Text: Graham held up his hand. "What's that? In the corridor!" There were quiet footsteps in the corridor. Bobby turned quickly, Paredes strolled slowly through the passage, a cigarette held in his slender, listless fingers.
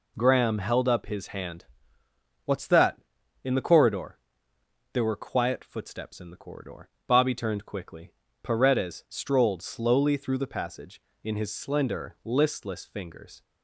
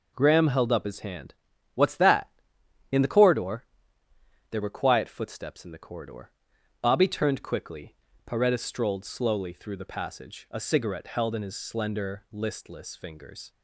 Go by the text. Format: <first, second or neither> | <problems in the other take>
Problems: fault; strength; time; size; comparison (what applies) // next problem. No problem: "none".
second | skips "a cigarette held"; at 11.1 s